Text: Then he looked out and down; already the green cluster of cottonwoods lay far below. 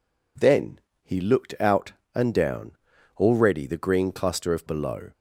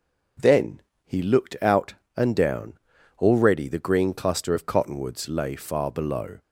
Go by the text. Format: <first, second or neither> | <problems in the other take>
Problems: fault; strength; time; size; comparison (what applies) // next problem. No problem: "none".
second | pauses between "Then" and "he"; slight; at 0.7 s; 0.24 s long; slight in the second // skips "cottonwoods lay far"; at 4.6 s